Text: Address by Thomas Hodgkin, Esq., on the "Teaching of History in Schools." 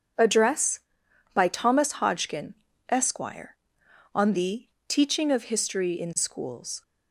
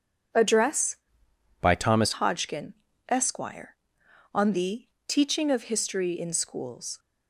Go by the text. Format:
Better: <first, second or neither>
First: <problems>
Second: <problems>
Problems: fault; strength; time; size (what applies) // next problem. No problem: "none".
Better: first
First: pauses between "the" and "Teaching"; slight; at 4.6 s; 0.18 s long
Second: changes voice from "by" to "Thomas"; from 1.5 to 2.1 s; 0.6 s long // pauses between "the" and "Teaching"; slight; at 4.8 s; 0.18 s long